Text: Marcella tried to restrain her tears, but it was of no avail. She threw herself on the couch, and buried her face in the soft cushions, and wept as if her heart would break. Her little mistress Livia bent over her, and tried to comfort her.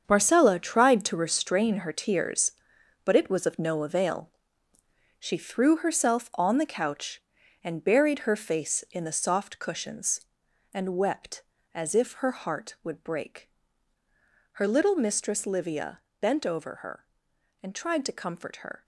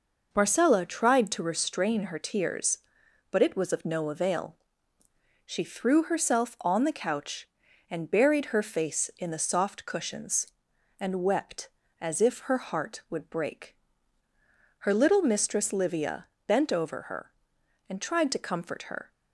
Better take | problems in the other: second | gets quieter; strong; throughout; 10.5 dB // pauses between "Livia" and "bent"; slight; at 16.0 s; 0.20 s long; slight in the second

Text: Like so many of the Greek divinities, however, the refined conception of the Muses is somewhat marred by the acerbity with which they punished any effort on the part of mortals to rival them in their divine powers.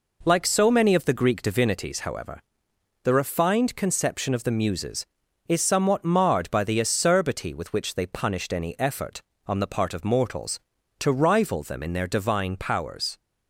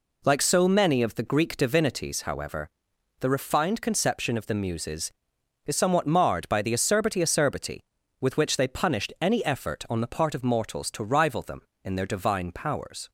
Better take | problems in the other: first | says "acerbity" twice; at 7.2 s

